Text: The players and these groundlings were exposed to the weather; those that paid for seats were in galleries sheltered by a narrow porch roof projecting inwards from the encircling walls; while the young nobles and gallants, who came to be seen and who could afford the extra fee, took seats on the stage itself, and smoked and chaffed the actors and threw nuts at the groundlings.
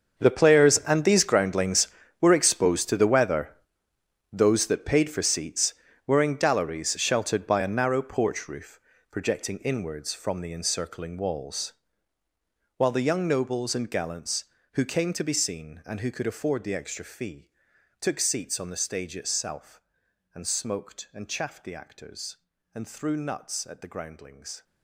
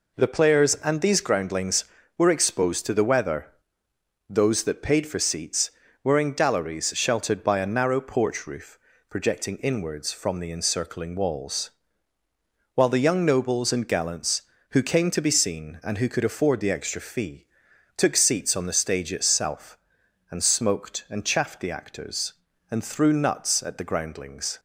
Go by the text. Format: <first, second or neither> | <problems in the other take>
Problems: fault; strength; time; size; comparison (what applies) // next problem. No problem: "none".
second | gets quieter; strong; throughout; 16.5 dB // pauses between "roof" and "projecting"; slight; at 8.7 s; 0.32 s long; slight in the second